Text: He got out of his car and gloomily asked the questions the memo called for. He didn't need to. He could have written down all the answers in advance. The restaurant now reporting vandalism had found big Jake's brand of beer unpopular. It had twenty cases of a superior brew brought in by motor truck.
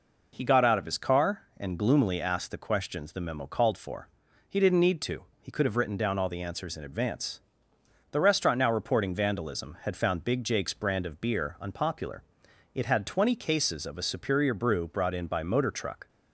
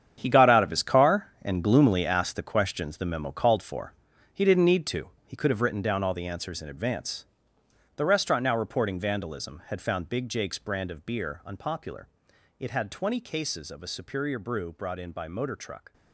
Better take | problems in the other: first | gets quieter; strong; throughout; 12 dB

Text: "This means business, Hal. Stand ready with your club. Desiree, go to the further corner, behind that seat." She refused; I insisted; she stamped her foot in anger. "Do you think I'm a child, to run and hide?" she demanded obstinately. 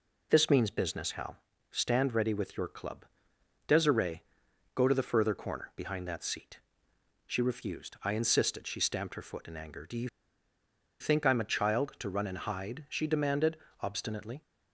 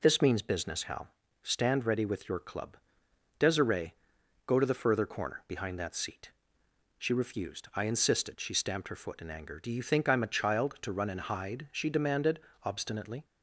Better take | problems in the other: second | pauses between "you" and "think"; noticeable; at 10.0 s; 0.93 s long // pauses between "demanded" and "obstinately"; slight; at 13.5 s; 0.26 s long; slight in the second

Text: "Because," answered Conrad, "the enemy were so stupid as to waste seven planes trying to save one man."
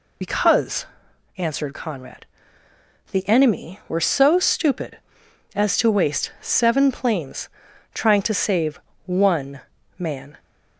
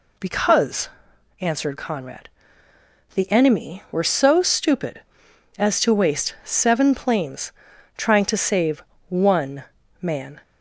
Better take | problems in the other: second | loses the start of "Because"; at 0.2 s; 55 ms // pauses between "planes" and "trying"; noticeable; at 7.4 s; 0.48 s long; noticeable in the second // pauses between "save" and "one"; slight; at 8.7 s; 0.26 s long; slight in the second // pauses between "one" and "man"; slight; at 9.6 s; 0.36 s long; slight in the second

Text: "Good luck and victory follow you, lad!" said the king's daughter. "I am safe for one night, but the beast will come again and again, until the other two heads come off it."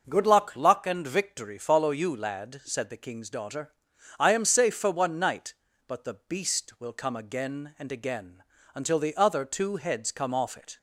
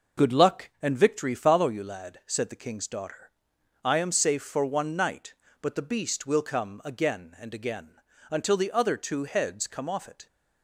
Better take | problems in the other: second | starts louder than the rest; noticeable; until 1.0 s; 6 dB // says "luck" twice; at 0.5 s

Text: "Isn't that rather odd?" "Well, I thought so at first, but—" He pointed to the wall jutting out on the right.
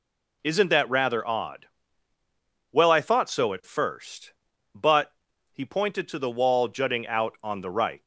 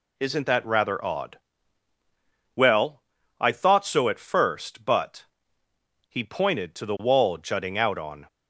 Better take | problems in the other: first | stops before "the right"; at 8.2 s

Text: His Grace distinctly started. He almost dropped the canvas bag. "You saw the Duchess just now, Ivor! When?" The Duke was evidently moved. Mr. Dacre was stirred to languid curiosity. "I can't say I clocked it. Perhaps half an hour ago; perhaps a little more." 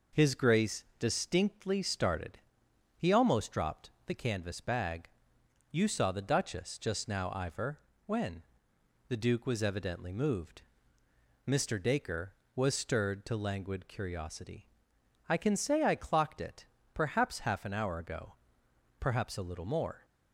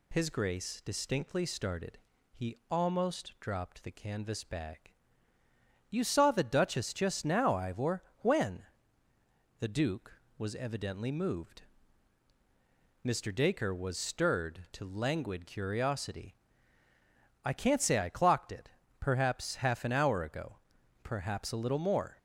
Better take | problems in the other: second | pauses between "Grace" and "distinctly"; slight; at 0.8 s; 0.16 s long // pauses between "dropped" and "the"; slight; at 3.8 s; 0.16 s long // says "can" for "can't"; at 15.3 s

